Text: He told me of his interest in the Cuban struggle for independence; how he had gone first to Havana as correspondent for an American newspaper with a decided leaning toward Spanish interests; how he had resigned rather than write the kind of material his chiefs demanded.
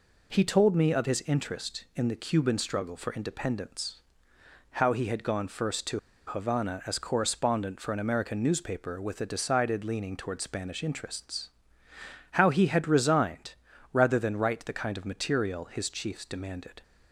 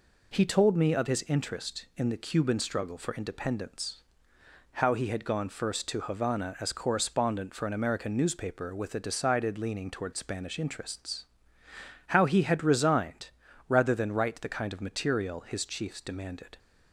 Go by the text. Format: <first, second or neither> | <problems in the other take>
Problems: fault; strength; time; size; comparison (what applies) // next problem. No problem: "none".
second | pauses between "to" and "Havana"; slight; at 5.9 s; 0.27 s long // pauses between "resigned" and "rather"; at 13.5 s; 0.38 s long; also in the second